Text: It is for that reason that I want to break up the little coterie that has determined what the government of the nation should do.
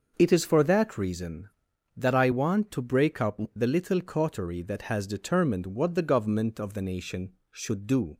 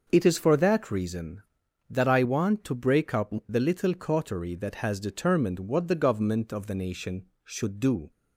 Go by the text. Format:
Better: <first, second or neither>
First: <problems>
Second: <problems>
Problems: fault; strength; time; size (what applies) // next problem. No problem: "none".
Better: neither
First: starts louder than the rest; until 1.1 s; 6 dB // pauses between "up" and "the"; slight; at 3.3 s; 0.16 s long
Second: starts louder than the rest; noticeable; until 1.1 s; 6 dB // pauses between "up" and "the"; slight; at 3.3 s; 0.16 s long